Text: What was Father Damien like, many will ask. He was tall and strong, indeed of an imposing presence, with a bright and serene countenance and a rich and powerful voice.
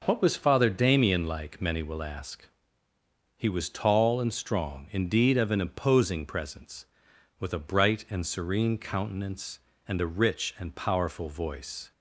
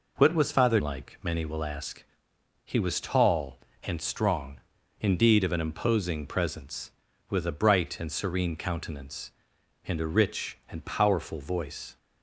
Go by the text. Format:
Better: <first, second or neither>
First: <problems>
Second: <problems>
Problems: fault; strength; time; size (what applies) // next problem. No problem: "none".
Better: first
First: none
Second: skips "Damien"; at 0.8 s